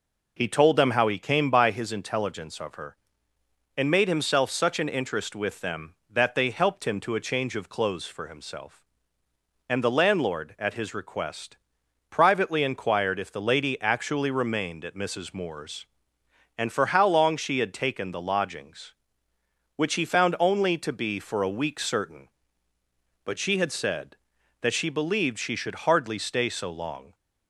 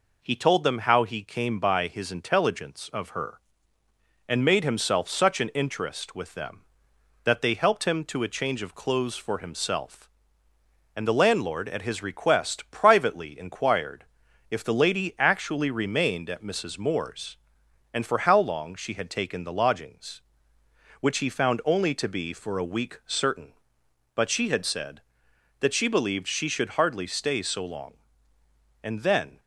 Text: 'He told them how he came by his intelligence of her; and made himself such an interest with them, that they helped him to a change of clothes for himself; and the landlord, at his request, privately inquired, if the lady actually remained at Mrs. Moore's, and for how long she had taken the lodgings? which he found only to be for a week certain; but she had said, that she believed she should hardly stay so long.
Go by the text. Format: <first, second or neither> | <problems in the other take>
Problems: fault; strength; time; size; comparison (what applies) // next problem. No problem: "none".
first | goes on to say "And then"; from 28.8 s on; 0.56 s long